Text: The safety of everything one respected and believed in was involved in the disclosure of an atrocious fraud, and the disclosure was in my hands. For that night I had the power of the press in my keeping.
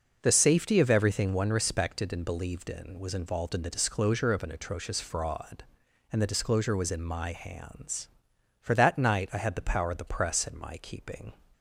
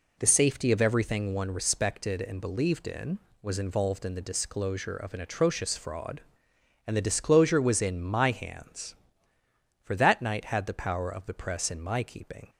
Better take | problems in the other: first | skips "I"; at 10.4 s

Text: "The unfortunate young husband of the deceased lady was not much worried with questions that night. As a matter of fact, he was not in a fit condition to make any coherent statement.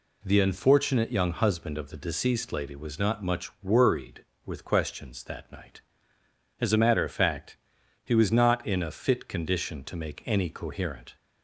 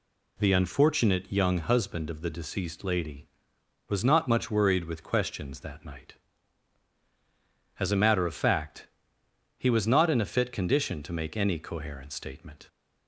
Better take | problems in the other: second | stops before "statement"; at 11.1 s

